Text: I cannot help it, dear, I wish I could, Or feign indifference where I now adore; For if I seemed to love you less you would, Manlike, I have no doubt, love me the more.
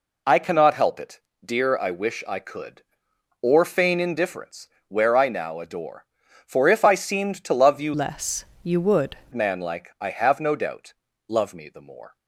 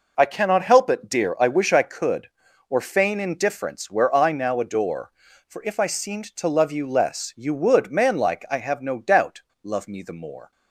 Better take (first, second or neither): second